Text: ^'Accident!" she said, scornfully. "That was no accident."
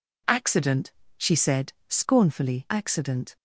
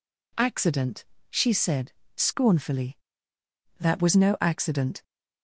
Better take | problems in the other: second | skips "That was no"; at 2.6 s

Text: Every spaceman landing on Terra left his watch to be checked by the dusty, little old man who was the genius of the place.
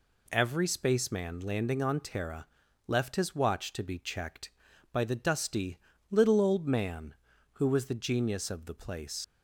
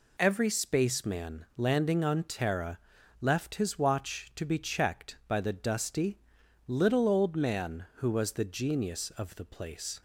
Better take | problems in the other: second | pauses between "Terra" and "left"; at 2.4 s; 0.40 s long; also in the second // leaves "place" unfinished; at 9.2 s; 100 ms

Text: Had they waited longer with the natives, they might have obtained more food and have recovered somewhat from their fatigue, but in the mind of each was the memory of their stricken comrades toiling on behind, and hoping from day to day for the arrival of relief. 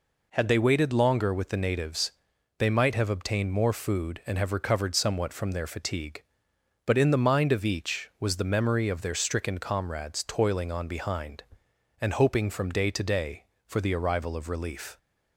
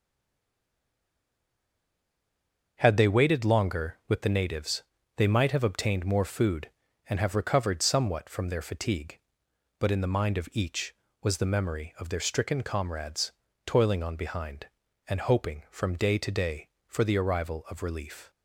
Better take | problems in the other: first | stays silent before the first word; strong; until 2.7 s; 2.7 s long // starts louder than the rest; until 3.8 s; 6.5 dB // pauses between "comrades" and "toiling"; slight; at 13.3 s; 0.32 s long

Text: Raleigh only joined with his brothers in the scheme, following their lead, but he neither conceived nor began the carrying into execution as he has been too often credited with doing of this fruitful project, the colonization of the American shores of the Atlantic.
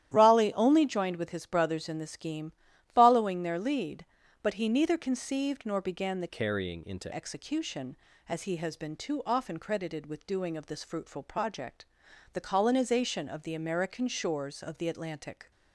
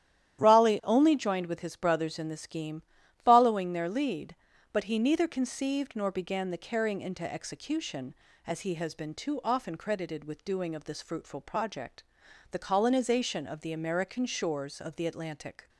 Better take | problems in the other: second | starts louder than the rest; strong; until 1.1 s; 12 dB; strong in the second // changes voice from "carrying" to "into"; from 6.2 to 7.1 s; 0.9 s long

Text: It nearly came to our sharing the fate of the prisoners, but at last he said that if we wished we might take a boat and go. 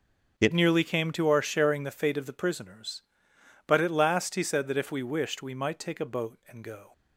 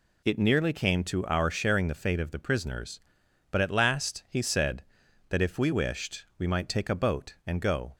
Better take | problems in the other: second | starts louder than the rest; until 1.4 s; 7 dB // changes voice at "nearly"; from 0.5 s on; 6.4 s long

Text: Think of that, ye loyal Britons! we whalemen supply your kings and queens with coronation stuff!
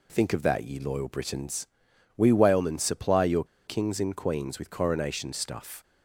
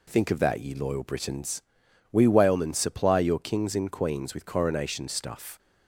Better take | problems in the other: second | pauses between "your" and "kings"; slight; at 3.4 s; 0.22 s long

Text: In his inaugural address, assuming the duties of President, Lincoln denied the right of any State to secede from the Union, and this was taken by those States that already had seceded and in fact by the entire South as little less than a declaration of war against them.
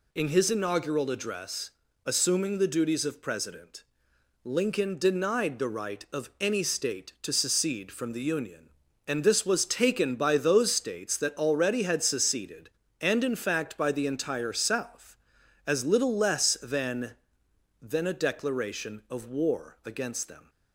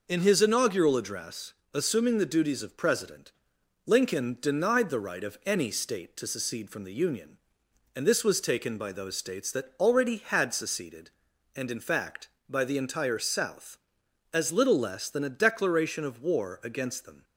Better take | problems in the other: second | says "than" twice; at 17.7 s

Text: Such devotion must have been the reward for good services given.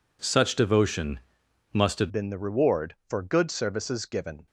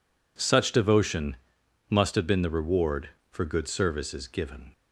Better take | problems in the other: second | pauses between "devotion" and "must"; noticeable; at 1.1 s; 0.54 s long; noticeable in the second // changes voice at "been"; from 2.1 s on; 2.3 s long

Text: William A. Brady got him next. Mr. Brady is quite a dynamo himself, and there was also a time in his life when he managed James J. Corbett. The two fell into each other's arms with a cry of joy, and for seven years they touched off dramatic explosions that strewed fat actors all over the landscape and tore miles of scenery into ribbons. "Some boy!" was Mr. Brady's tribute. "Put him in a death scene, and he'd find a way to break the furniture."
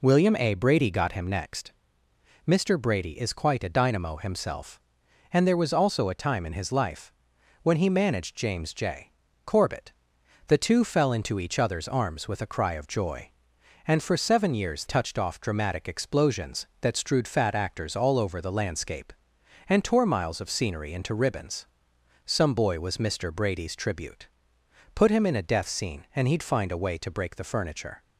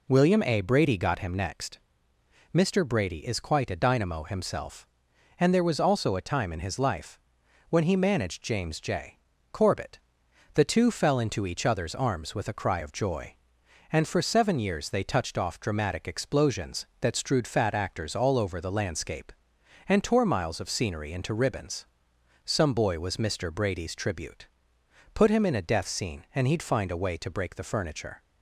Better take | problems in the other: second | pauses between "life" and "when"; noticeable; at 7.1 s; 0.50 s long; noticeable in the second // skips "they"; at 14.8 s

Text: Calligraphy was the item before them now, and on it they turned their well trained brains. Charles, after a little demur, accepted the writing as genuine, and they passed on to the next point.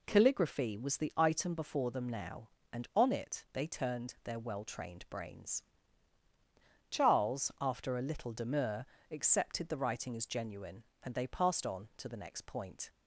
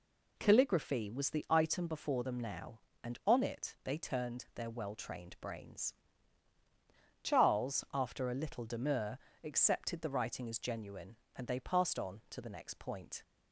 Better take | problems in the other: neither | none

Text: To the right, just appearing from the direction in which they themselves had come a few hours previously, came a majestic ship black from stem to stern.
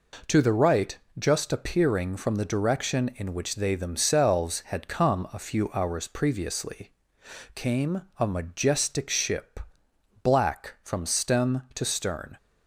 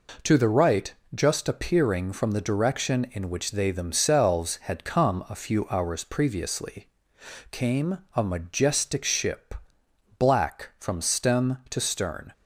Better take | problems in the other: neither | pauses between "came" and "a"; slight; the same in both // pauses between "ship" and "black"; noticeable; the same in both

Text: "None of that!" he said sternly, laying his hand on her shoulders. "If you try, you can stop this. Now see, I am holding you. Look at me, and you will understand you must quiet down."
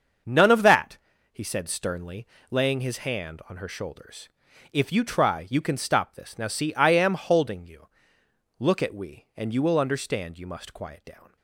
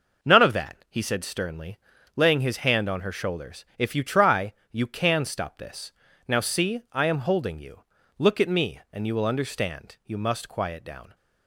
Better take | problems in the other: second | starts louder than the rest; until 1.6 s; 6.5 dB // says "we" for "me"; at 8.9 s

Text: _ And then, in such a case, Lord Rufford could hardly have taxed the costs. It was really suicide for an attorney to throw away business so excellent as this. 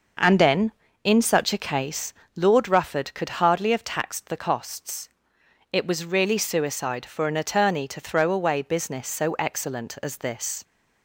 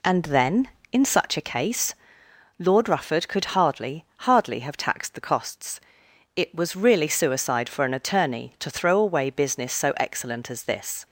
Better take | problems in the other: first | says "hardly" twice; at 4.1 s

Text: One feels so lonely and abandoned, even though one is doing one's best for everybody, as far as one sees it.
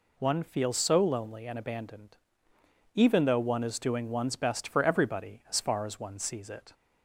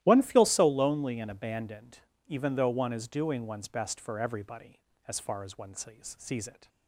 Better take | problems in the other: first | starts louder than the rest; strong; until 1.0 s; 14 dB // says "sees" twice; at 6.1 s

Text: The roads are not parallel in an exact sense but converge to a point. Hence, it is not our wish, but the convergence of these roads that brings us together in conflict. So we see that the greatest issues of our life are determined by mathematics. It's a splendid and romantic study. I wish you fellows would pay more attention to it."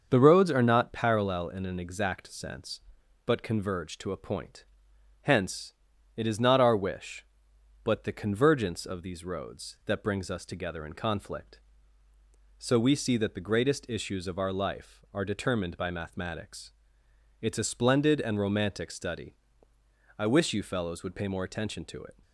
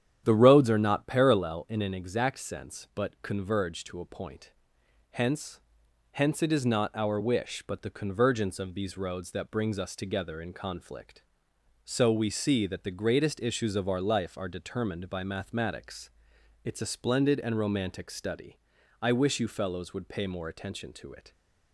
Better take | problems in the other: first | starts louder than the rest; strong; until 1.2 s; 9.5 dB; also in the first // says "Hence" twice; at 6.1 s

